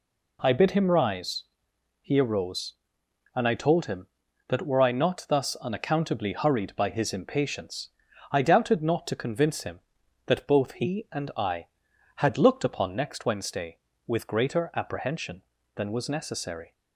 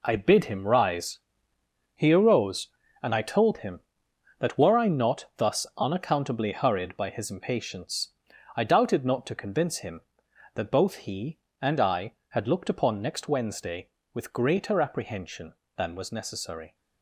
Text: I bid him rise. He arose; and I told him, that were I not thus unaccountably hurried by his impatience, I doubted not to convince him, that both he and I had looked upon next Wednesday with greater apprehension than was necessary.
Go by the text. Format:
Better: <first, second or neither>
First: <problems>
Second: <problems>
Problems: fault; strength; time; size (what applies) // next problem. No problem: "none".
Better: first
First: none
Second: gets quieter; strong; throughout; 9 dB